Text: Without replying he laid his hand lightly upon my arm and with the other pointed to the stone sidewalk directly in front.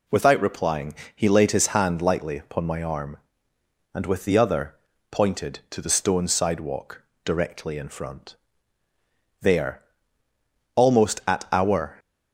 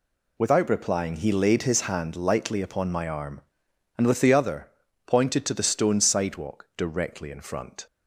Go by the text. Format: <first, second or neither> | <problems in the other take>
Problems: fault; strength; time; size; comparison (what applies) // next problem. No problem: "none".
second | pauses between "replying" and "he"; slight; at 0.9 s; 0.20 s long // pauses between "other" and "pointed"; slight; at 4.7 s; 0.36 s long; slight in the second // pauses between "sidewalk" and "directly"; slight; at 7.0 s; 0.24 s long // goes on to say "There almost at our"; strong; from 9.4 s on; 2.5 s long